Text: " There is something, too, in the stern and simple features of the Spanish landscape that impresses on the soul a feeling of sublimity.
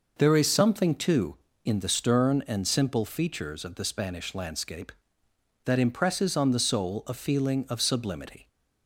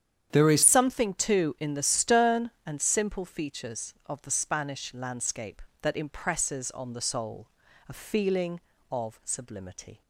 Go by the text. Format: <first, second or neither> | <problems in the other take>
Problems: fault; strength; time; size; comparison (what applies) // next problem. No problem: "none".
first | starts louder than the rest; strong; until 1.3 s; 9 dB // changes voice at "something"; from 0.6 s on; 9.4 s long // pauses between "soul" and "a"; at 7.4 s; 0.40 s long